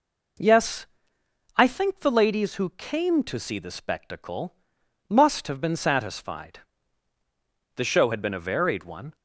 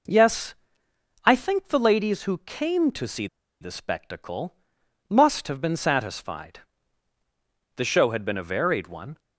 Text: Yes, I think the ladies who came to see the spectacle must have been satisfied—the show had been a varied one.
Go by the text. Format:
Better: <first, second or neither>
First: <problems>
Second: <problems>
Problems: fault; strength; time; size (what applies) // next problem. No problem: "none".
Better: first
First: pauses between "spectacle" and "must"; noticeable; at 4.5 s; 0.54 s long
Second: pauses between "see" and "the"; slight; at 3.2 s; 0.34 s long // pauses between "spectacle" and "must"; noticeable; at 4.5 s; 0.54 s long